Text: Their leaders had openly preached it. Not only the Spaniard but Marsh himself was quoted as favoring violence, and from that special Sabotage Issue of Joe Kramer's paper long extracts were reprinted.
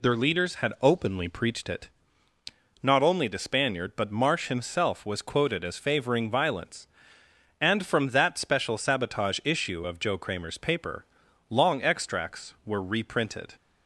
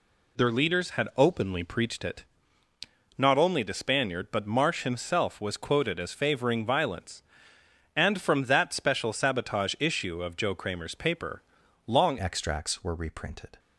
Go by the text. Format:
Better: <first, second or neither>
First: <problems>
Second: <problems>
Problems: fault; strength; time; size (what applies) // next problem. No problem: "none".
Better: first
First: pauses between "paper" and "long"; noticeable; at 11.0 s; 0.46 s long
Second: pauses between "paper" and "long"; noticeable; at 11.4 s; 0.46 s long // changes voice at "extracts"; from 12.1 s on; 1.4 s long